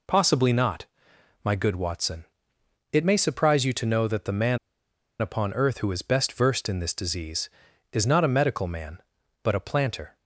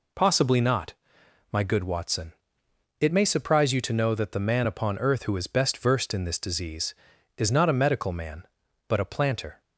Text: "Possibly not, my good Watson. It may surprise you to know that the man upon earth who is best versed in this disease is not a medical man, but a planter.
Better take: second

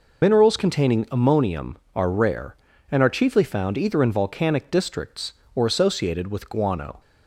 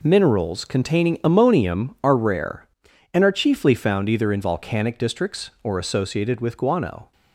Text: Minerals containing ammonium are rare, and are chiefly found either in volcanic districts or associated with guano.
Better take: second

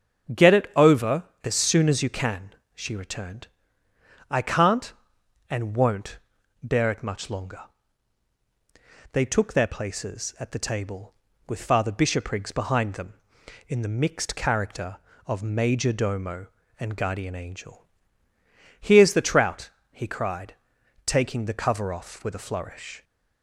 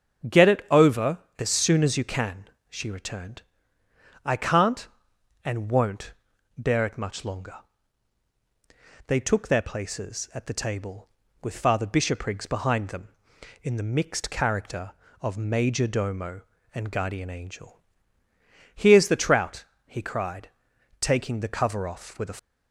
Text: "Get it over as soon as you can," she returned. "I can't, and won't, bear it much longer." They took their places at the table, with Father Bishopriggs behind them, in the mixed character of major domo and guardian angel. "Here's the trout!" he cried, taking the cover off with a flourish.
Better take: first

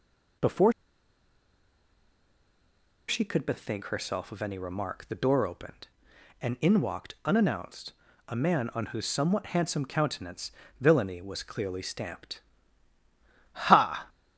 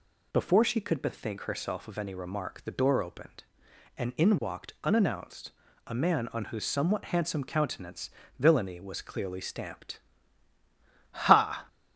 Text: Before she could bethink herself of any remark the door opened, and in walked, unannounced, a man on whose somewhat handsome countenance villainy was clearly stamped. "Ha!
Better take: second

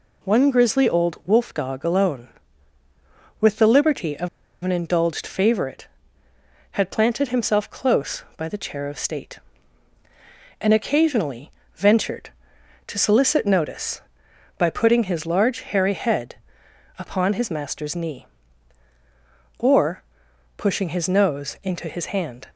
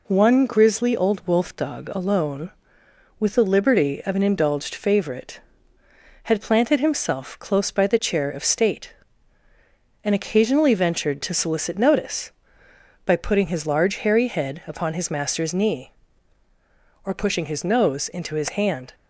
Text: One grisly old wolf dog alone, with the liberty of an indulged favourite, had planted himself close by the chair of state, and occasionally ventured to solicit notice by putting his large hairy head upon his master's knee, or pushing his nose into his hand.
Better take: second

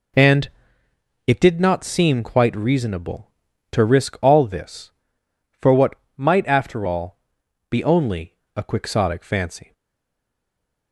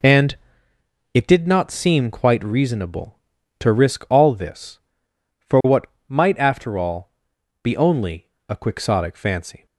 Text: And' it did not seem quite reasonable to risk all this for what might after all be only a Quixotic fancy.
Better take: second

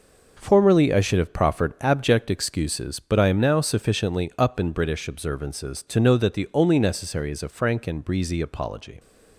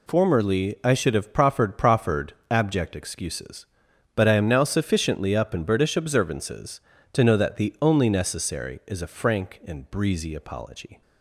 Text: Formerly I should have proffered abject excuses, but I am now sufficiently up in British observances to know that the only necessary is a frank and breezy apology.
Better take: first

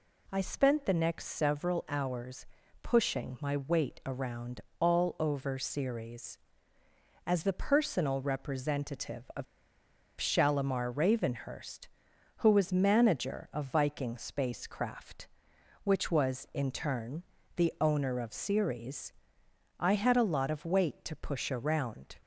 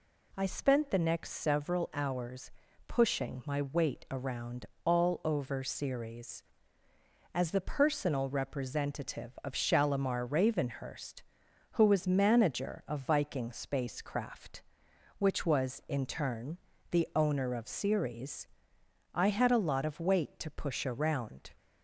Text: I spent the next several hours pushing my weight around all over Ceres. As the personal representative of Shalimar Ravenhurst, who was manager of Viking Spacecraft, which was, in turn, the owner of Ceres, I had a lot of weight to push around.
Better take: second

